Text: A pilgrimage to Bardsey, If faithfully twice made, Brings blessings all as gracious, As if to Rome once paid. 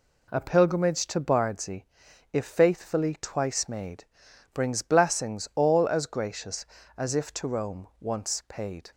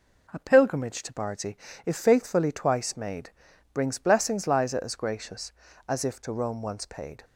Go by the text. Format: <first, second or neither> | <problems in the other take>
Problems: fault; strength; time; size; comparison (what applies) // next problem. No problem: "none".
first | says "liza" for "all"; at 4.4 s